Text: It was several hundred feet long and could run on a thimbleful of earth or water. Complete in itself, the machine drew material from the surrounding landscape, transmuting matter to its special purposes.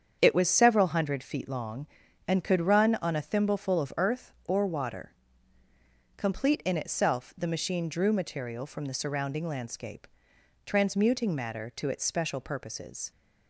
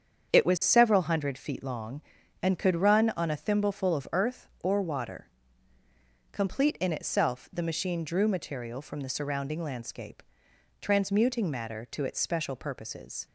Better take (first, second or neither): neither